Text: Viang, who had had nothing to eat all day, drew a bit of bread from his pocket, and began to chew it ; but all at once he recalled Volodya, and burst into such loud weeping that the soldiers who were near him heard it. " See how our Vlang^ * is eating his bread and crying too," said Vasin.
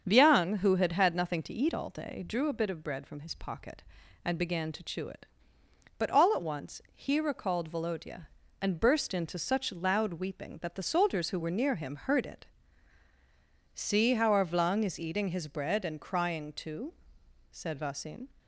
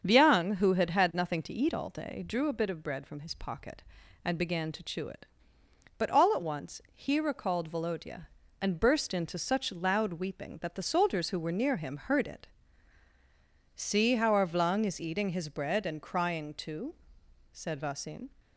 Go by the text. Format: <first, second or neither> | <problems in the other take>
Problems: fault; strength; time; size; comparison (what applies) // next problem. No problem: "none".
neither | starts louder than the rest; strong; the same in both